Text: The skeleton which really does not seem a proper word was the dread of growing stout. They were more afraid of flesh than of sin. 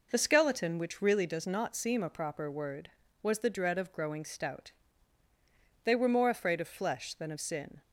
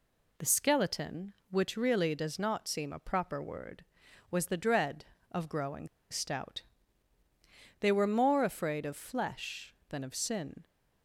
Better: first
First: none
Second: pauses between "growing" and "stout"; slight; at 5.8 s; 0.22 s long

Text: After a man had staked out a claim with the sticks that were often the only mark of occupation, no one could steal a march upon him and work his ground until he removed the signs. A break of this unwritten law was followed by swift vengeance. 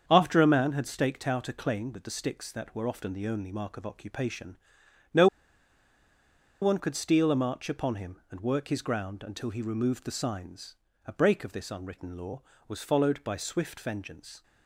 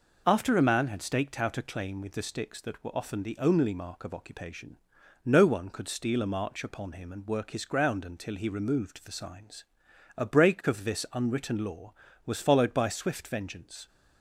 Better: second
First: starts louder than the rest; strong; until 1.0 s; 7.5 dB // pauses between "no" and "one"; strong; at 5.2 s; 1.3 s long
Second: none

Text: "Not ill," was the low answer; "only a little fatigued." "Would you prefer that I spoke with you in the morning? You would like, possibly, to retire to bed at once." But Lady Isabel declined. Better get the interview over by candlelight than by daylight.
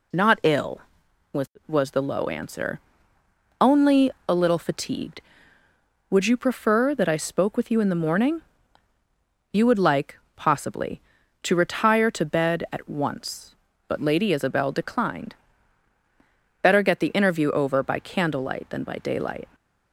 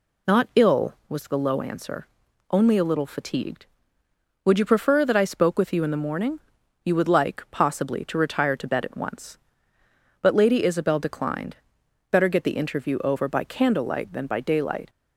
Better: second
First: says "was" twice; at 1.6 s // pauses between "only" and "a"; slight; at 4.1 s; 0.16 s long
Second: none

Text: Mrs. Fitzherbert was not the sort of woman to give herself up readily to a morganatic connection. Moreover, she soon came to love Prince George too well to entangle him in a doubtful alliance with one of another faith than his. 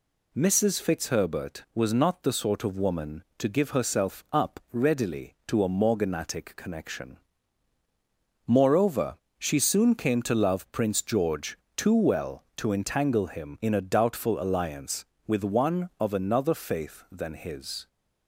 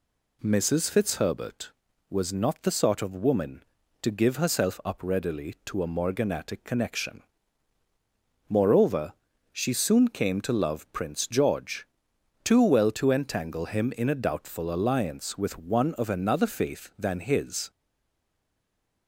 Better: first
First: pauses between "George" and "too"; slight; at 11.5 s; 0.18 s long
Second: pauses between "George" and "too"; noticeable; at 11.8 s; 0.56 s long // stays silent after the last word; noticeable; from 17.7 s on; 1.3 s long

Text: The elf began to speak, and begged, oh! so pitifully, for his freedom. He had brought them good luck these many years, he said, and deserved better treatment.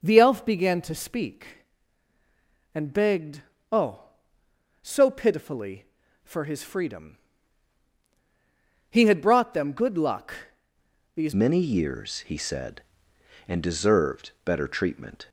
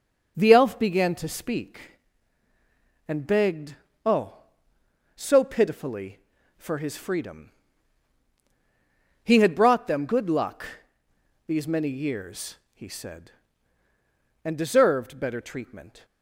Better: second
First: pauses between "luck" and "these"; noticeable; at 10.3 s; 0.80 s long // changes voice at "many"; from 11.3 s on; 3.9 s long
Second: pauses between "luck" and "these"; noticeable; at 10.6 s; 0.80 s long

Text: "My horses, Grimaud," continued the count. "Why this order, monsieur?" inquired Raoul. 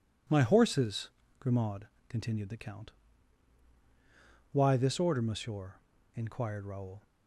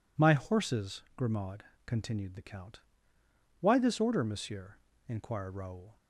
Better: neither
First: none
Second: none

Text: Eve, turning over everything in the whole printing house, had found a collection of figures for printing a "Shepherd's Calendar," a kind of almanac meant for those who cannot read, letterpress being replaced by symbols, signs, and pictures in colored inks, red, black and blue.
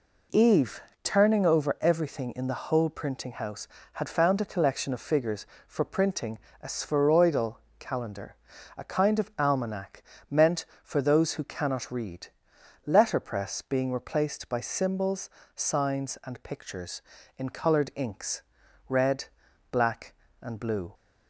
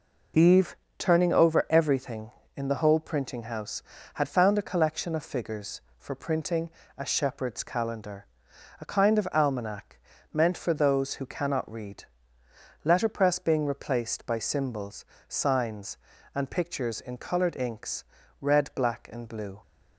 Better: second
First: pauses between "printing" and "a"; slight; at 6.3 s; 0.24 s long // says "Spheroidal" for "Shepherd's"; at 6.6 s // pauses between "almanac" and "meant"; slight; at 10.0 s; 0.26 s long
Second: pauses between "printing" and "a"; slight; at 6.6 s; 0.28 s long // pauses between "almanac" and "meant"; slight; at 9.9 s; 0.36 s long

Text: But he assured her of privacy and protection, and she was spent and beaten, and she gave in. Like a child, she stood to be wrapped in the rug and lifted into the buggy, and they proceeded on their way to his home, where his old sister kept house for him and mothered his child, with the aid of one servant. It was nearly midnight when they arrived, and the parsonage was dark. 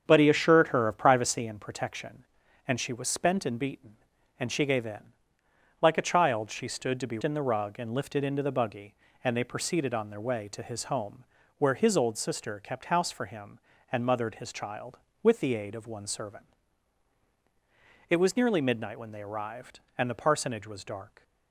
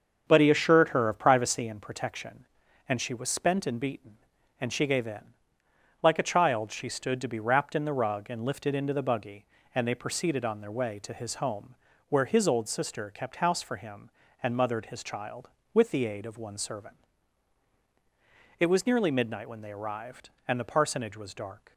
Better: second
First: starts louder than the rest; strong; until 1.0 s; 7.5 dB // skips "wrapped"; at 7.2 s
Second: starts louder than the rest; until 1.2 s; 7 dB

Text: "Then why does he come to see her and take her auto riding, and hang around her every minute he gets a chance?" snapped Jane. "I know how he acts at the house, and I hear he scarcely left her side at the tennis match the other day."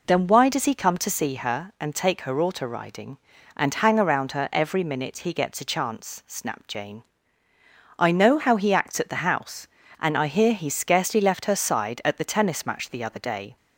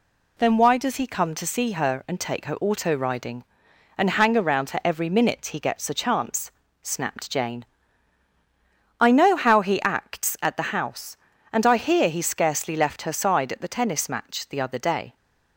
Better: neither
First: none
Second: none

